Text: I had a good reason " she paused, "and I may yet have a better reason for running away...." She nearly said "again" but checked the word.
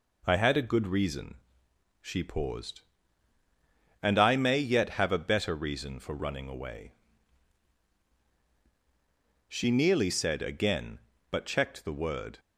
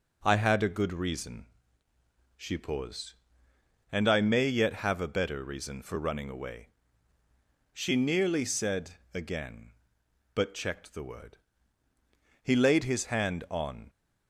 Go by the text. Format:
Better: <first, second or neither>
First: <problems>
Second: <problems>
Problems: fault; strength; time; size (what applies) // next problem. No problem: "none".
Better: first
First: none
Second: goes on to say "He laid his hand on"; from 12.4 s on; 1.4 s long